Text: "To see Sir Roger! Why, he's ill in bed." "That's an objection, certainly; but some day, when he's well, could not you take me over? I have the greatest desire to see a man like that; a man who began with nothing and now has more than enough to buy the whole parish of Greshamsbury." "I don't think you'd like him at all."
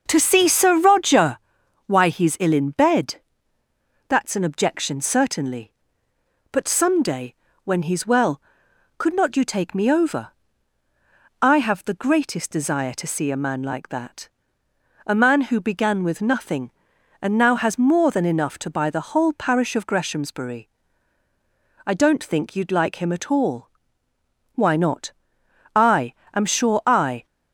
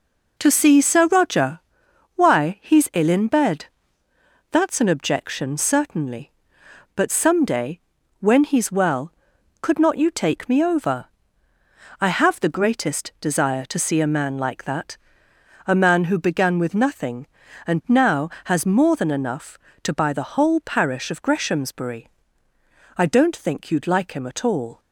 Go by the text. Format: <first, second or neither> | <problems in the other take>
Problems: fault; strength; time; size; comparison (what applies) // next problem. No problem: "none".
second | starts louder than the rest; noticeable; until 1.0 s; 6 dB // goes on to say "Why not I am sure I"; strong; from 24.5 s on; 2.7 s long